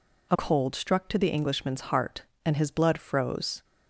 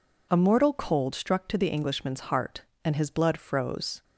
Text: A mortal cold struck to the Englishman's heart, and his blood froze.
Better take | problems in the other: second | skips "mortal"; at 0.3 s

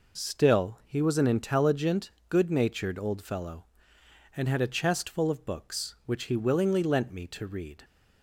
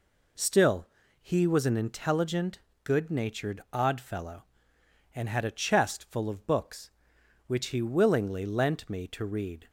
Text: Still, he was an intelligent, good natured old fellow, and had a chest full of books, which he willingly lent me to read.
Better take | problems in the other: first | says "odd" for "old"; at 3.7 s

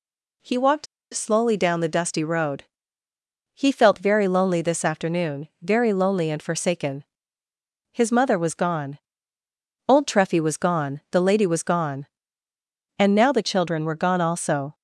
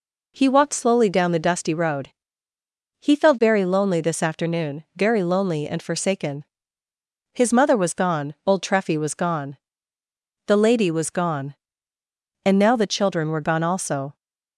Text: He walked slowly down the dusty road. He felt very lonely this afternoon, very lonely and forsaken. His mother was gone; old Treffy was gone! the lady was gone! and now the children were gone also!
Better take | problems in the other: second | pauses between "walked" and "slowly"; slight; at 0.8 s; 0.28 s long

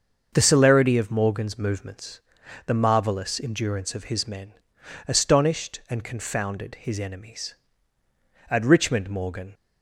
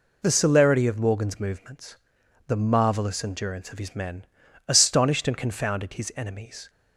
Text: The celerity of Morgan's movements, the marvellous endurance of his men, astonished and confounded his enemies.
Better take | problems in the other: second | starts louder than the rest; until 1.3 s; 6.5 dB // goes on to say "At Richmond Morgan"; noticeable; from 8.4 s on; 1.0 s long

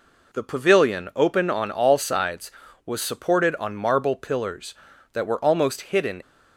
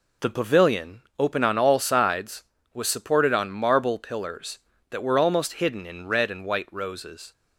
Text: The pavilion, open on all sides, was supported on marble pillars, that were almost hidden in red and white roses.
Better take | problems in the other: second | stops before "in red and white roses"; at 6.2 s

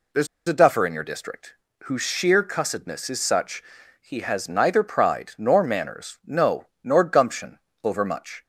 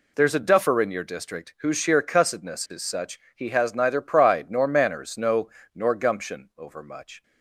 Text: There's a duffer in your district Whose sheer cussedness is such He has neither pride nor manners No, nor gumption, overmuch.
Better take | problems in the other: second | pauses between "There's" and "a"; slight; at 0.2 s; 0.21 s long // pauses between "district" and "Whose"; slight; at 1.5 s; 0.30 s long // pauses between "such" and "He"; at 3.6 s; 0.38 s long; slight in the second

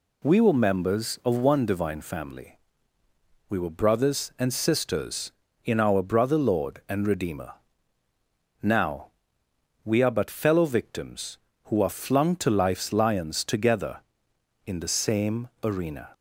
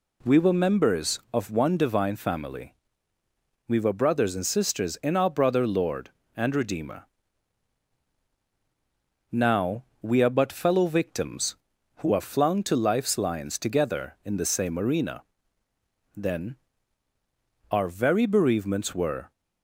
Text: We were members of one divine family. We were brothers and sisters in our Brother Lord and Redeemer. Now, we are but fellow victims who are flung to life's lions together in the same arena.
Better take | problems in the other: first | goes on to say "Then our very bereavements were"; strong; from 16.1 s on; 3.1 s long

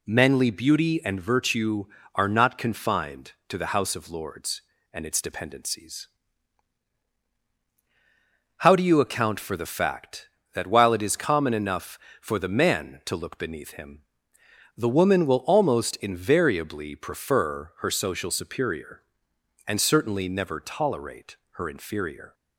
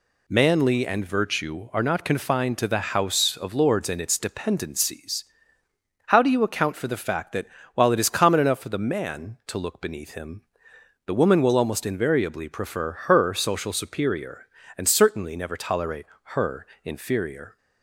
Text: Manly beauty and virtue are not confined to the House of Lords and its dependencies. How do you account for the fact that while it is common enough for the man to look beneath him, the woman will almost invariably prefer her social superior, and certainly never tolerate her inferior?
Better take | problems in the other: first | skips "beauty"; at 0.8 s // pauses between "that" and "while"; slight; at 7.4 s; 0.28 s long // pauses between "tolerate" and "her"; slight; at 16.0 s; 0.28 s long; slight in the first // pauses between "her" and "inferior"; slight; at 16.6 s; 0.18 s long

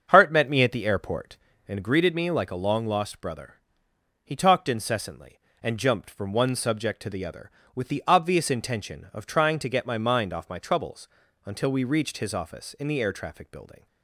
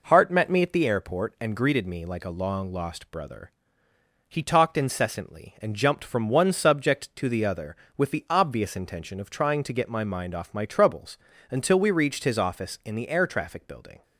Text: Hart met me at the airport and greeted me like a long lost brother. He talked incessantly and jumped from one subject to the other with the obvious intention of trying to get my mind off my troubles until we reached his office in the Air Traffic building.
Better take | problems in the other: second | starts louder than the rest; until 1.7 s; 7 dB // pauses between "troubles" and "until"; slight; at 11.0 s; 0.36 s long; slight in the second

